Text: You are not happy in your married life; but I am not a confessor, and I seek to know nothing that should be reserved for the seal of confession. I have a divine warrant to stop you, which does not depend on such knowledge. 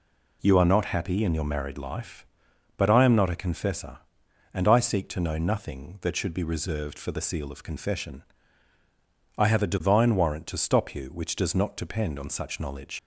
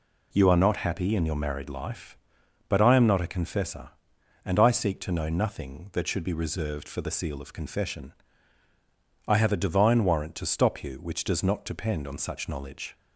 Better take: second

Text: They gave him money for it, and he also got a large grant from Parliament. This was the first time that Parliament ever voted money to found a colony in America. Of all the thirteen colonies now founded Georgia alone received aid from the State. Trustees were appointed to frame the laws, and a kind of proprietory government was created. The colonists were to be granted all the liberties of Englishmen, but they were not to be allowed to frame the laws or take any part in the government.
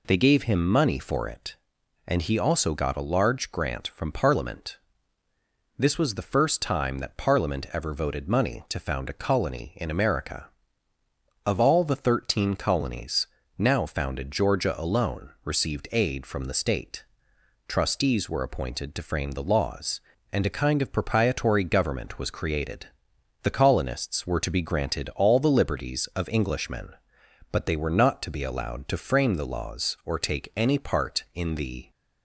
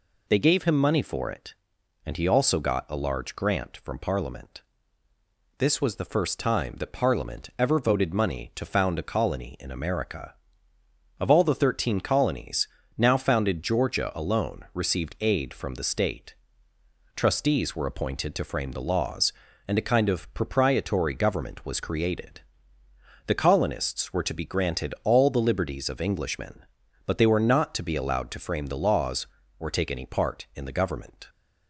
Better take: second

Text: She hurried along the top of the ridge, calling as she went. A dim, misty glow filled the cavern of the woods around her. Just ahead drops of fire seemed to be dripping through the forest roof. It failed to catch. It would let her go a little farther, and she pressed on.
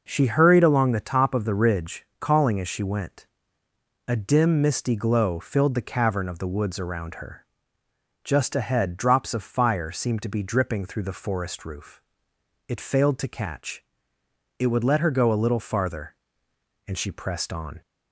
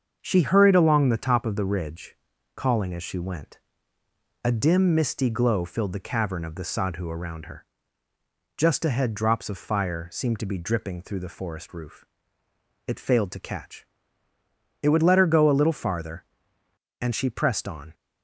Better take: first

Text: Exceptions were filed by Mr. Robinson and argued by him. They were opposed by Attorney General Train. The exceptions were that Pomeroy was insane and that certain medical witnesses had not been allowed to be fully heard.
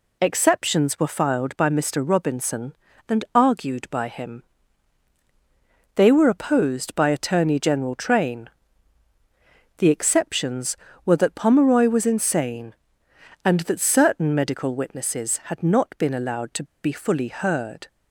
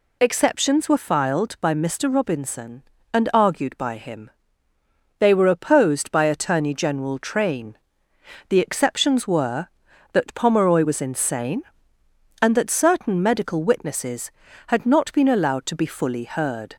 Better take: second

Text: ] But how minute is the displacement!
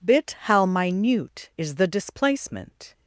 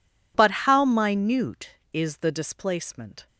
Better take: second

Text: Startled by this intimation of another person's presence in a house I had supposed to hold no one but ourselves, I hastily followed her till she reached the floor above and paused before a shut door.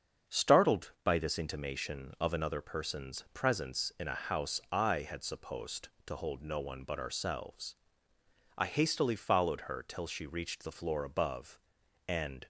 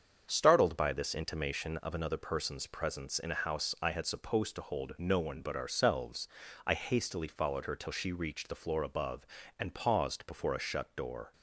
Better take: second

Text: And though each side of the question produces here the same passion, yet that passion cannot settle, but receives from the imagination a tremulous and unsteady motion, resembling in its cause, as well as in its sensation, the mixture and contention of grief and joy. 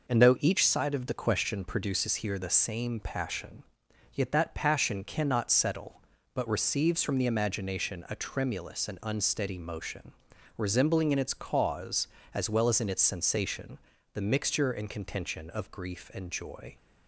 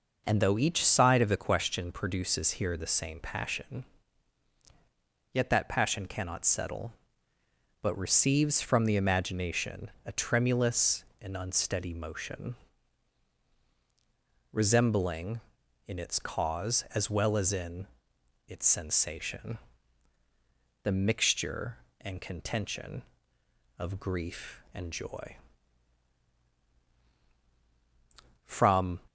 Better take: first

